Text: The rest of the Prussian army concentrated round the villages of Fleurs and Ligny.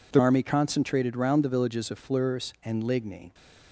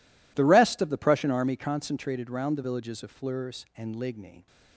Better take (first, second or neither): second